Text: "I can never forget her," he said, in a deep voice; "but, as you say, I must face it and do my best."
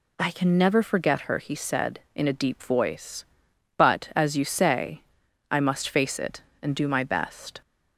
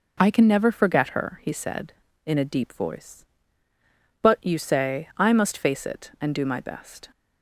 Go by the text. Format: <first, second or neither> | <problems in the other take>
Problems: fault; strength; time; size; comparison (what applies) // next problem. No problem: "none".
first | skips "as"; at 4.4 s